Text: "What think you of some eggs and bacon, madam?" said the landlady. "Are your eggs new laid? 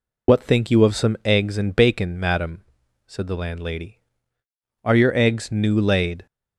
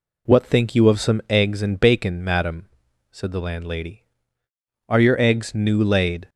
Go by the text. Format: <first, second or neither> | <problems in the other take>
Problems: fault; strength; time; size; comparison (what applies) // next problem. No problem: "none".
second | loses the start of "What"; at 0.2 s; 50 ms